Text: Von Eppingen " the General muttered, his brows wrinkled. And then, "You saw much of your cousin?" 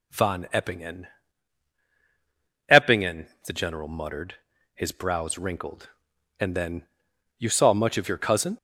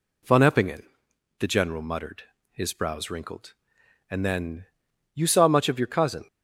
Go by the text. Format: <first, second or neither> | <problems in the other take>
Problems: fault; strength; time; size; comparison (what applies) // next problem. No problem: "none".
second | says "Eppingen" twice; at 2.7 s